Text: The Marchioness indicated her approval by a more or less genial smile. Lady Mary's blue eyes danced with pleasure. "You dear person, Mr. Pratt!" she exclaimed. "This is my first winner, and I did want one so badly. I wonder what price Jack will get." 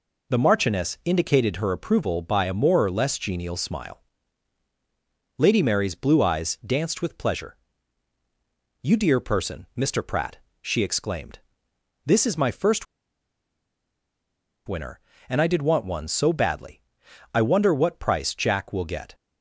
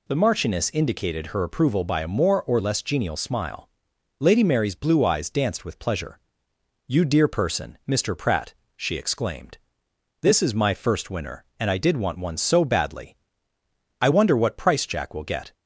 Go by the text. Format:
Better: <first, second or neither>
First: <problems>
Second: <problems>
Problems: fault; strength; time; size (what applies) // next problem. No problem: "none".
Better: second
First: pauses between "first" and "winner"; strong; at 12.8 s; 1.8 s long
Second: none